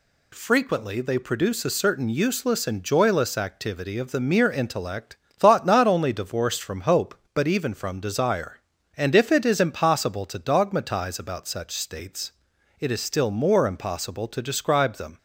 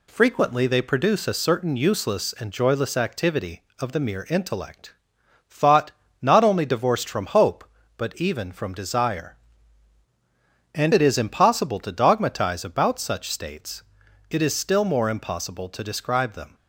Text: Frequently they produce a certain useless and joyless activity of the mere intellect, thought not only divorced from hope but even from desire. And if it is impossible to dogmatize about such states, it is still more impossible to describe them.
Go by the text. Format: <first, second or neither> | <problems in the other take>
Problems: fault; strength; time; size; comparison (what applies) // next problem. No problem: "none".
first | pauses between "thought" and "not"; slight; at 5.9 s; 0.28 s long // skips "if"; at 10.9 s